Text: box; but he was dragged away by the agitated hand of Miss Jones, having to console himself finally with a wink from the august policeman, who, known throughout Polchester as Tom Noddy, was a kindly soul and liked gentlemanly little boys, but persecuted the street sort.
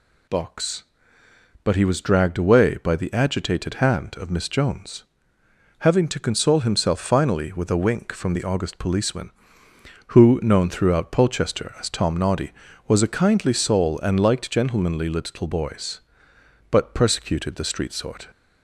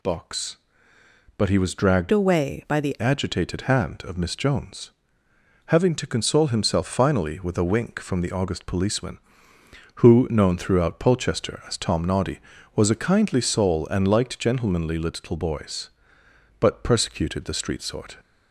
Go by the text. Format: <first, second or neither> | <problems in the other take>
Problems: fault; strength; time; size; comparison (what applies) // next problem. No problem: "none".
first | changes voice from "away" to "the"; from 2.1 to 2.9 s; 0.8 s long